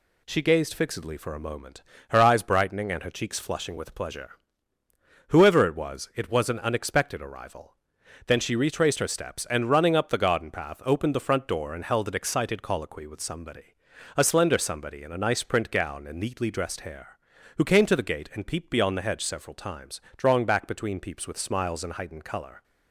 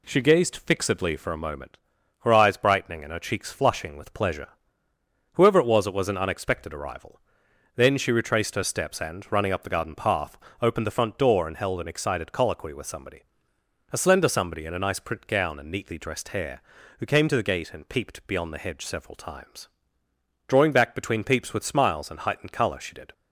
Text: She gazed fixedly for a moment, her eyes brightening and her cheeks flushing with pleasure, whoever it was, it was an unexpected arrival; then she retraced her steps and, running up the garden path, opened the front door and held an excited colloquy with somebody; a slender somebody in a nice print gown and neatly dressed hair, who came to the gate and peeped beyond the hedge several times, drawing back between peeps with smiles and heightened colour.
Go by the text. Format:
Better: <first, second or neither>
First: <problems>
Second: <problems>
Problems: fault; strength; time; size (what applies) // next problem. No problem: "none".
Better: first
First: none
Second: goes on to say "She did"; slight; from 22.8 s on; 0.32 s long